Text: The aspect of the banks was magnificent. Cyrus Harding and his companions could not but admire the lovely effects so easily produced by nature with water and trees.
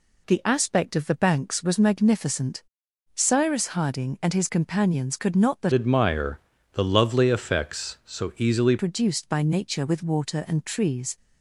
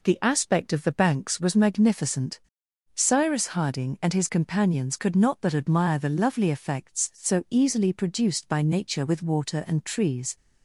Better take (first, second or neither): second